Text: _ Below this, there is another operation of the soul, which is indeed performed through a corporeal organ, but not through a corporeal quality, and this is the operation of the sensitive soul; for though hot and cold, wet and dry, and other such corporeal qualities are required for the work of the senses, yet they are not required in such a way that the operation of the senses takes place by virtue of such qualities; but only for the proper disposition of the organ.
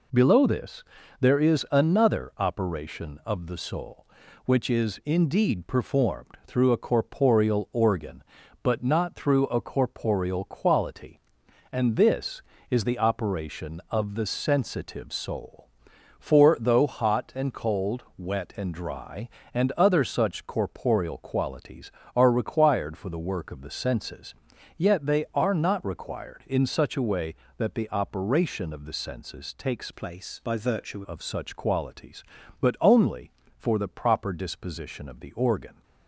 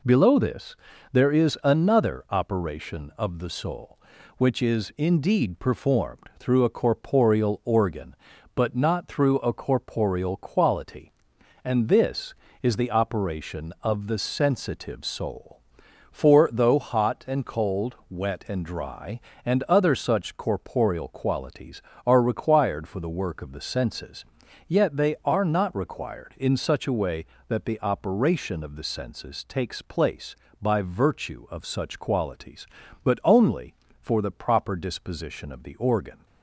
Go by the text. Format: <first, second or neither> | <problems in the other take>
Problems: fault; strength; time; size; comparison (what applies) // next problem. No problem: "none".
second | changes voice from "place" to "virtue"; from 29.9 to 31.0 s; 1.1 s long